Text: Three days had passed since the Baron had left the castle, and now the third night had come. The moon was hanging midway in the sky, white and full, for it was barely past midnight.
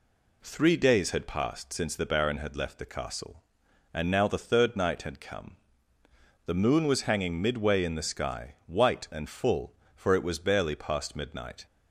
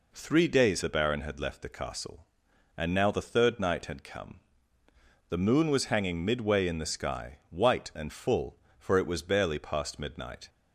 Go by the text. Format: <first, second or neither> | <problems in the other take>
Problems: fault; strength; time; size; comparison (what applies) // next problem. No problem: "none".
first | skips "had passed since"; at 0.8 s